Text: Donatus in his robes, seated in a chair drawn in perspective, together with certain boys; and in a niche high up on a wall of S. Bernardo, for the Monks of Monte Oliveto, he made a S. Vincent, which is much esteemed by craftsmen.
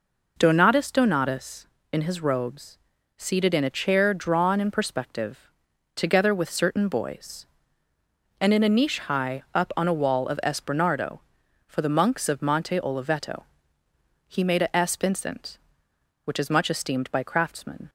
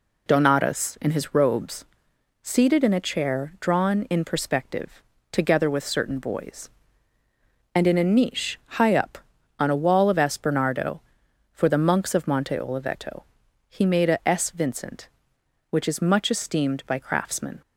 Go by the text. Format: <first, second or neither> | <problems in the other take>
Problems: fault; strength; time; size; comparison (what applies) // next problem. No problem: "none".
second | says "Donatus" twice; at 0.9 s